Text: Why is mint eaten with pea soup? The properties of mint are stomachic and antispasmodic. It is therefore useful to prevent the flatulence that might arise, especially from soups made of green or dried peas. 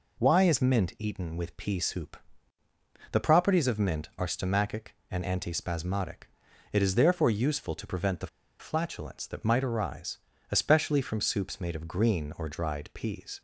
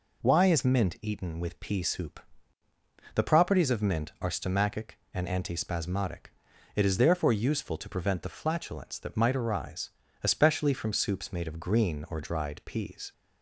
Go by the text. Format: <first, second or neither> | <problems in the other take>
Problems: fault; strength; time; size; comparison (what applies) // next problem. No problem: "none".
second | pauses between "the" and "flatulence"; slight; at 8.2 s; 0.33 s long